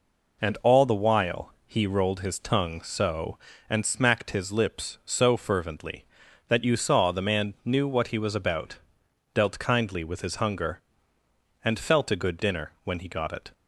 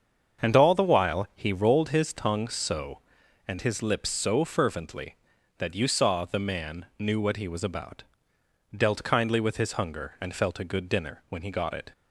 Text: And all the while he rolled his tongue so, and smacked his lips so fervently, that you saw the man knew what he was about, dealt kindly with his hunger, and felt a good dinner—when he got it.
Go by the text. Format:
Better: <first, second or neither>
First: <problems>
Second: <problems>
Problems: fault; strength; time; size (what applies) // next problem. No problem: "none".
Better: first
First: none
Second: starts louder than the rest; until 1.5 s; 7 dB // skips "smacked"; at 3.6 s